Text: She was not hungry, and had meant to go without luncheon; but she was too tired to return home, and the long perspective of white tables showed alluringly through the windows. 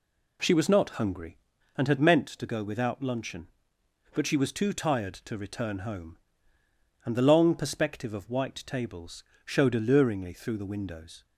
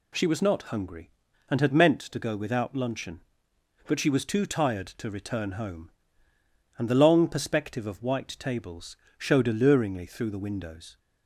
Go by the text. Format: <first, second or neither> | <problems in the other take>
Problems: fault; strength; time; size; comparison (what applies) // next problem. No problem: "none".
second | starts louder than the rest; slight; until 1.5 s; 2 dB // pauses between "tables" and "showed"; slight; at 9.2 s; 0.22 s long; slight in the second